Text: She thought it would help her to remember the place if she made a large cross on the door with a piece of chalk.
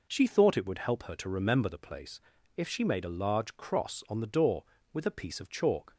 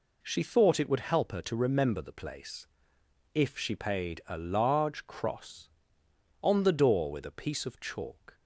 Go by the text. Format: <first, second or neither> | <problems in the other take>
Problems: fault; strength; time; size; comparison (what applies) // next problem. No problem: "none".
first | pauses between "place" and "if"; noticeable; at 2.6 s; 0.66 s long; slight in the first // says "paid" for "made"; at 3.7 s